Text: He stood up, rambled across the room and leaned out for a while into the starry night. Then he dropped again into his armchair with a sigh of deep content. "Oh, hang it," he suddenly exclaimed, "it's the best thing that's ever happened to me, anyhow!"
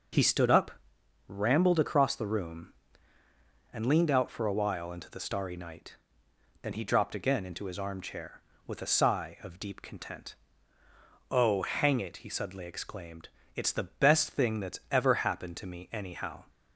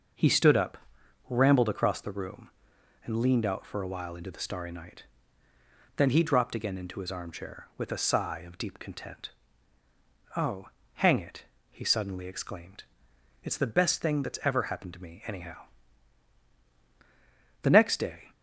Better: first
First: none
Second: starts louder than the rest; until 1.6 s; 6 dB // goes on to say "The next day"; noticeable; from 17.6 s on; 0.70 s long

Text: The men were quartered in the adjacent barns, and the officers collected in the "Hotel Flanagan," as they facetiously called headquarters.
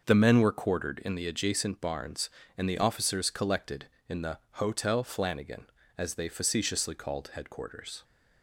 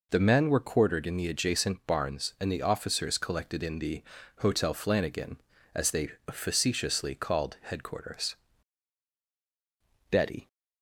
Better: first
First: pauses between "the" and "Hotel"; slight; at 4.3 s; 0.16 s long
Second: pauses between "the" and "Hotel"; slight; at 4.0 s; 0.34 s long // pauses between "they" and "facetiously"; slight; at 6.0 s; 0.18 s long // goes on to say "Betty"; slight; from 10.1 s on; 0.36 s long

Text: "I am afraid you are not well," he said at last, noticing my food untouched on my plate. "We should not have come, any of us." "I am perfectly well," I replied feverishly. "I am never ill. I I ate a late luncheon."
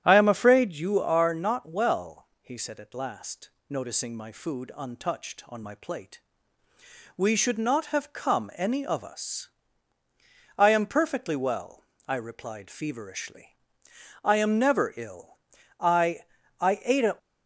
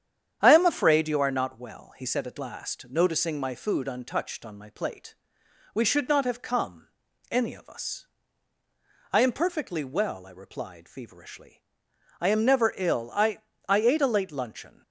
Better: second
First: starts louder than the rest; strong; until 1.0 s; 10 dB // pauses between "I" and "I"; at 16.1 s; 0.40 s long // stops before "late luncheon"; at 17.1 s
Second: starts louder than the rest; strong; until 1.4 s; 9 dB // pauses between "I" and "I"; slight; at 13.4 s; 0.28 s long

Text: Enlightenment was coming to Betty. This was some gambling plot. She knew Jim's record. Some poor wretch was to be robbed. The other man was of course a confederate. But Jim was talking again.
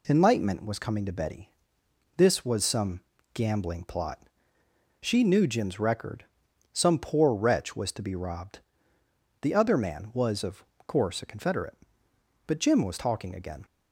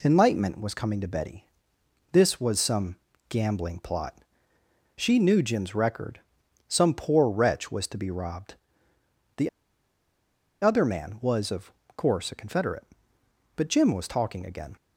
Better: first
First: pauses between "some" and "gambling"; slight; at 2.9 s; 0.34 s long // pauses between "of" and "course"; slight; at 10.6 s; 0.22 s long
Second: pauses between "some" and "gambling"; slight; at 2.9 s; 0.34 s long // pauses between "The" and "other"; at 9.4 s; 1.1 s long // pauses between "of" and "course"; slight; at 11.7 s; 0.24 s long

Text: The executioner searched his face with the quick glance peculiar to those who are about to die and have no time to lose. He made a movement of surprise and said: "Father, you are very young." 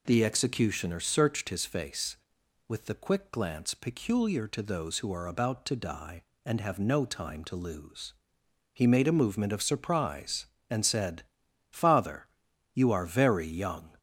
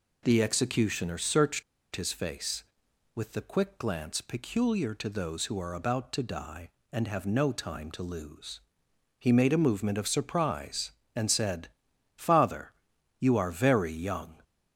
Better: first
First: none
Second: pauses between "searched" and "his"; slight; at 1.6 s; 0.31 s long

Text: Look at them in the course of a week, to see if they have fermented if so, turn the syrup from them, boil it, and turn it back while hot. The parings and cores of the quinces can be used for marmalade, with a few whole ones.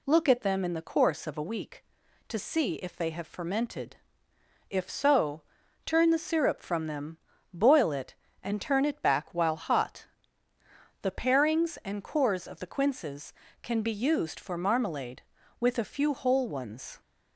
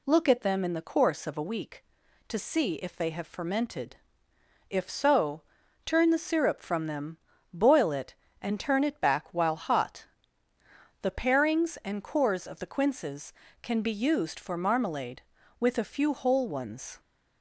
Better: neither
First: pauses between "fermented" and "if"; noticeable; at 3.9 s; 0.72 s long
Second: pauses between "fermented" and "if"; noticeable; at 3.9 s; 0.72 s long

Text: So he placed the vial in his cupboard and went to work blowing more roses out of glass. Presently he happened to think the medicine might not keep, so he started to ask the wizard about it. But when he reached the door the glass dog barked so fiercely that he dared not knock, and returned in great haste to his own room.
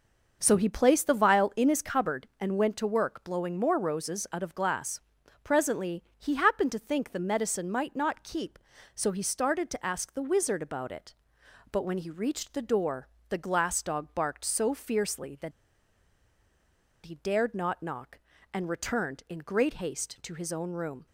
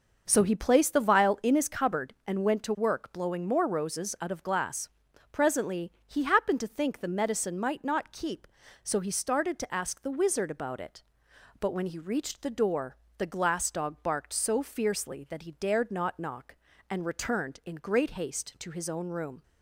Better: second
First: starts louder than the rest; noticeable; until 1.4 s; 6 dB // pauses between "Presently" and "he"; slight; at 6.0 s; 0.16 s long // pauses between "door" and "the"; slight; at 13.0 s; 0.20 s long // pauses between "that" and "he"; strong; at 15.5 s; 1.5 s long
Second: starts louder than the rest; noticeable; until 1.2 s; 6 dB // pauses between "Presently" and "he"; slight; at 5.9 s; 0.16 s long // pauses between "door" and "the"; slight; at 12.9 s; 0.20 s long

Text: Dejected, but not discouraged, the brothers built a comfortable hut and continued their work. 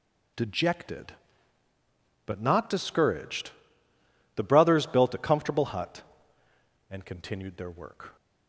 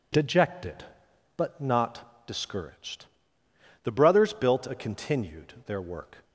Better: first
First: none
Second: skips "comfortable hut and"; at 4.7 s

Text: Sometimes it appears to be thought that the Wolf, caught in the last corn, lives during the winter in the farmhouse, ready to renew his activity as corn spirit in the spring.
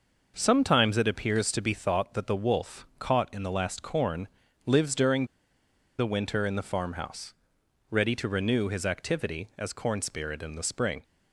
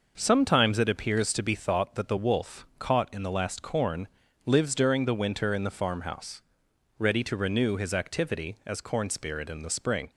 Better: second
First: pauses between "during" and "the"; noticeable; at 5.2 s; 0.71 s long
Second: none

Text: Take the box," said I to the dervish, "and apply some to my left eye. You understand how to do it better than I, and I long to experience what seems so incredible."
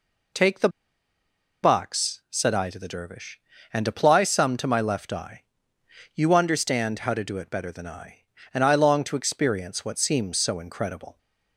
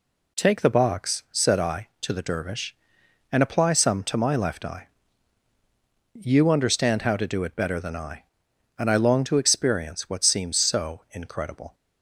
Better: second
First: pauses between "the" and "box"; noticeable; at 0.6 s; 0.93 s long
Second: none

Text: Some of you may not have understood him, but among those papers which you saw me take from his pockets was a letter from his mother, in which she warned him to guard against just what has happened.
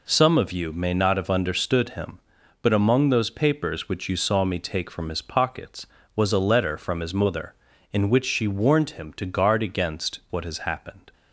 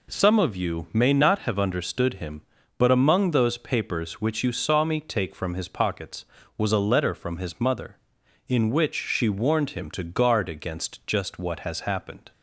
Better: second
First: skips "just"; at 10.2 s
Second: none

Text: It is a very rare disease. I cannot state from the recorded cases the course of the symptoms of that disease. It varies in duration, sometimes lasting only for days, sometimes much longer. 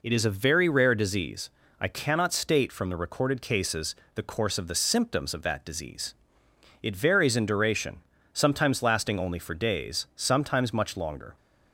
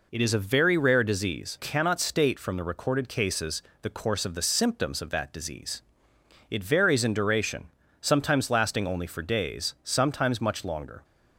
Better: first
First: pauses between "cases" and "the"; slight; at 3.9 s; 0.20 s long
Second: skips "I"; at 1.5 s // pauses between "cases" and "the"; slight; at 3.6 s; 0.20 s long

